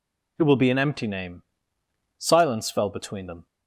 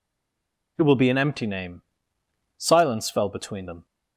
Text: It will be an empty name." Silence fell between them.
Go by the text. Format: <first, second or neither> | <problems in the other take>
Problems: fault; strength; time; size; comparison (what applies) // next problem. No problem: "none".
first | stays silent before the first word; slight; until 0.7 s; 0.7 s long